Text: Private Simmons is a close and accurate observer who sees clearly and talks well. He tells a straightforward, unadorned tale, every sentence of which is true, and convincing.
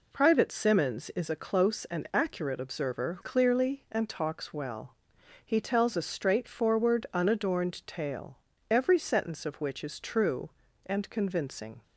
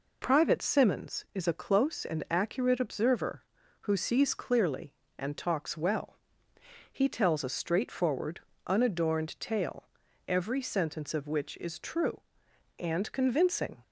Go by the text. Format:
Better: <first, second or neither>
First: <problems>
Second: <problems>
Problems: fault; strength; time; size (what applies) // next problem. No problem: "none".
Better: second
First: skips "who sees"; at 3.1 s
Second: none